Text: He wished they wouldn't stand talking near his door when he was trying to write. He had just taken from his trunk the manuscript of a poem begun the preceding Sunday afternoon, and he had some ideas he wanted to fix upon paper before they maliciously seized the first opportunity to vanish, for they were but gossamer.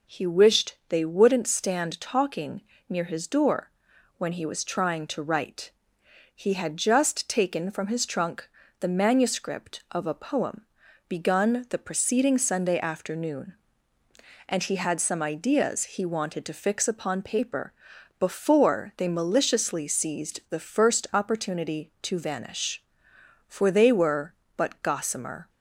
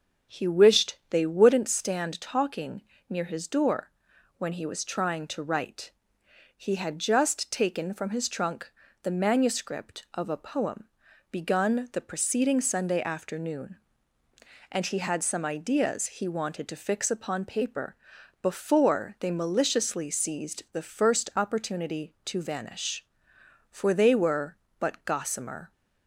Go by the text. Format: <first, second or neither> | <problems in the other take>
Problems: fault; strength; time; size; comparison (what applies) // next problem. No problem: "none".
first | starts louder than the rest; until 1.8 s; 6.5 dB // pauses between "talking" and "near"; slight; at 2.8 s; 0.26 s long; slight in the first // pauses between "door" and "when"; noticeable; at 3.8 s; 0.48 s long; noticeable in the first // pauses between "trunk" and "the"; slight; at 8.6 s; 0.34 s long; slight in the first // pauses between "poem" and "begun"; at 10.8 s; 0.42 s long; also in the first // pauses between "paper" and "before"; noticeable; at 17.9 s; 0.46 s long; noticeable in the first